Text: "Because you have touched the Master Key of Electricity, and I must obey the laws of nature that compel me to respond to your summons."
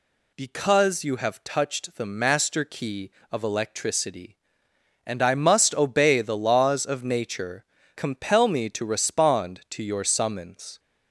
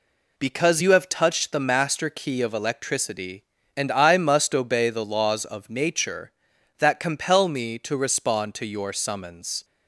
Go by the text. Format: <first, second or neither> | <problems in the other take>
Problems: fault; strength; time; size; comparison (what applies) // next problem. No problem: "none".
second | skips "that"; at 7.8 s